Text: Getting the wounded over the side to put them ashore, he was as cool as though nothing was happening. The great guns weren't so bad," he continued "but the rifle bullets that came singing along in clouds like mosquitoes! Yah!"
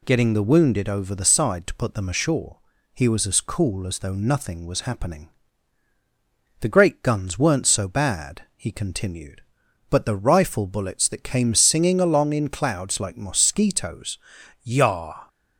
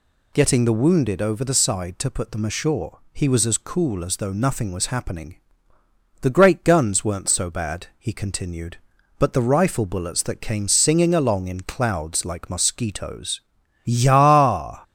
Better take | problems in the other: neither | none

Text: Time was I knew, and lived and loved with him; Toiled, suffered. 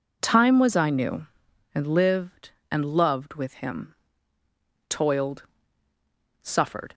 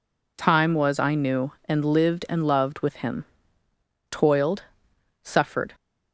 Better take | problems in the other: neither | none

